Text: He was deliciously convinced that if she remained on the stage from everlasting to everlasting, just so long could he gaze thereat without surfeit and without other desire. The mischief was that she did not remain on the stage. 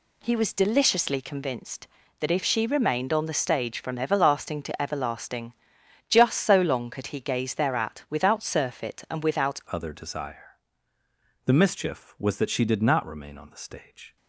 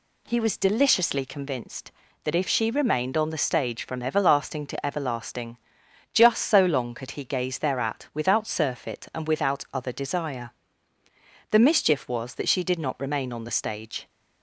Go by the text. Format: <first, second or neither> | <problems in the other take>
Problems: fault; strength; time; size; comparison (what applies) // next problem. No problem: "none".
second | changes voice at "other"; from 9.6 s on; 4.5 s long